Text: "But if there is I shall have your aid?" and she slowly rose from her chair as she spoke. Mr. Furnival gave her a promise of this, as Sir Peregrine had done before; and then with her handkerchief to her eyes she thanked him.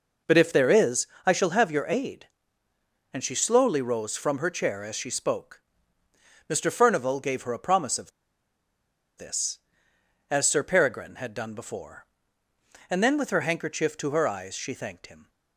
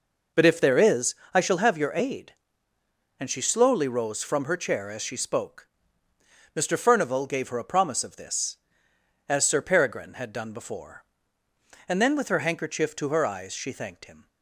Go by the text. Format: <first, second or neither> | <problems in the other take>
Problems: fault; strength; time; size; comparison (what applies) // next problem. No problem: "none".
second | pauses between "is" and "I"; slight; at 1.0 s; 0.20 s long; slight in the second // pauses between "of" and "this"; at 8.1 s; 1.0 s long